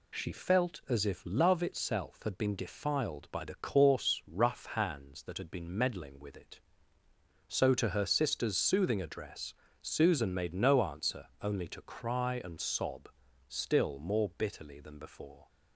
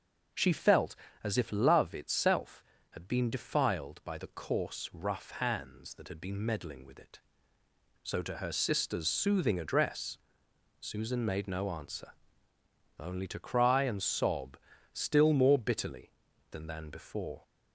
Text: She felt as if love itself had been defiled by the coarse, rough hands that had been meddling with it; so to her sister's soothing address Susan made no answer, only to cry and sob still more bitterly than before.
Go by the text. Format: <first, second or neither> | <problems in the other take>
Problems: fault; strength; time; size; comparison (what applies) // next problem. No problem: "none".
first | pauses between "address" and "Susan"; noticeable; at 10.1 s; 0.62 s long; slight in the first // pauses between "sob" and "still"; slight; at 14.5 s; 0.36 s long; also in the first // says "than" twice; at 16.6 s